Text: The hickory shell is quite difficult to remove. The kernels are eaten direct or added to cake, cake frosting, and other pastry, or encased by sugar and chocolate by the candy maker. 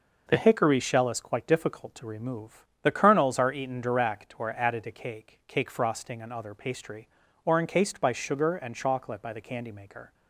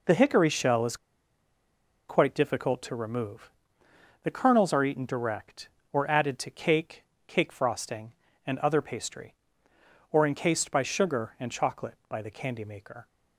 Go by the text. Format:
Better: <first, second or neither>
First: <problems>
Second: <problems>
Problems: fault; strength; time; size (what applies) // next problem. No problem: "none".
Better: first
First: none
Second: pauses between "is" and "quite"; at 0.9 s; 1.1 s long